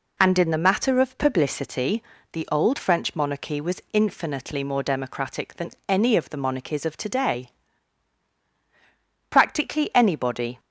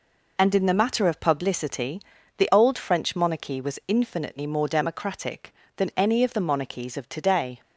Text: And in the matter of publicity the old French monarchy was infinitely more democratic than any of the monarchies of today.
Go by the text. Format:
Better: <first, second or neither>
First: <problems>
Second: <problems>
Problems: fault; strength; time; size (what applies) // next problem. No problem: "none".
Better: second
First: pauses between "publicity" and "the"; slight; at 2.0 s; 0.30 s long // pauses between "than" and "any"; slight; at 5.7 s; 0.16 s long // goes on to say "Practically anybody"; noticeable; from 9.2 s on; 1.3 s long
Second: pauses between "publicity" and "the"; at 1.9 s; 0.38 s long